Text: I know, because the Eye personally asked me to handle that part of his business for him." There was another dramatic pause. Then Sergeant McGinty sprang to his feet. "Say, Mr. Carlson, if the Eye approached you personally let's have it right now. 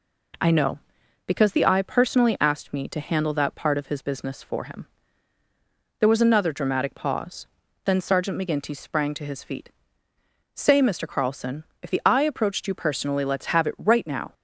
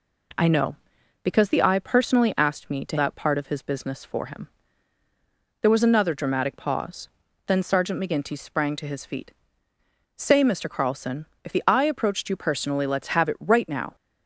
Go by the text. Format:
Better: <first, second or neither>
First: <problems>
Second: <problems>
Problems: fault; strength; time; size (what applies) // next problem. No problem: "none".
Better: first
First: none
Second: skips "handle"; at 2.9 s